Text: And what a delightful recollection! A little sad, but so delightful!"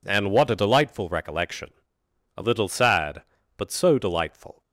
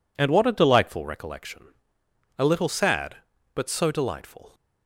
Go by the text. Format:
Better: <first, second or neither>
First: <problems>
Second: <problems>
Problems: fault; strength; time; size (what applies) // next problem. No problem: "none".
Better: neither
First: none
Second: none